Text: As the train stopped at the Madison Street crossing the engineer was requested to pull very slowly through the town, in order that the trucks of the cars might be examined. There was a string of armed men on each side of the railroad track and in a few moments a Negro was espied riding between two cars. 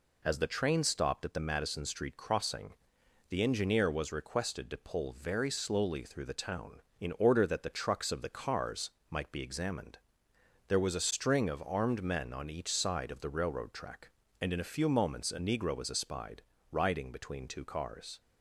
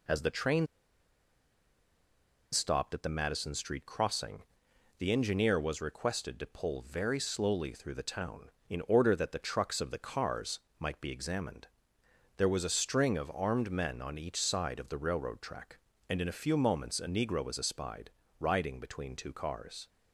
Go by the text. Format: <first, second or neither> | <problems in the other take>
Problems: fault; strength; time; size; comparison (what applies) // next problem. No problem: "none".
first | pauses between "train" and "stopped"; strong; at 0.6 s; 1.8 s long // pauses between "crossing" and "the"; noticeable; at 4.4 s; 0.56 s long; noticeable in the first // pauses between "cars" and "might"; slight; at 10.6 s; 0.18 s long; slight in the first // pauses between "espied" and "riding"; slight; at 18.1 s; 0.28 s long; slight in the first